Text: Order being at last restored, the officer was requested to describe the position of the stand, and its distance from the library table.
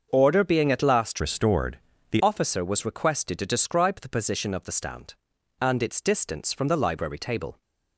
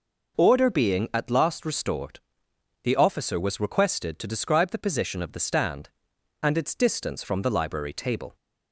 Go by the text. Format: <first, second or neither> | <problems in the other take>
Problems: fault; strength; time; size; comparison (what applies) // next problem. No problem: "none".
second | starts louder than the rest; until 1.1 s; 6.5 dB // changes voice from "restored" to "the"; from 1.1 to 2.2 s; 1.1 s long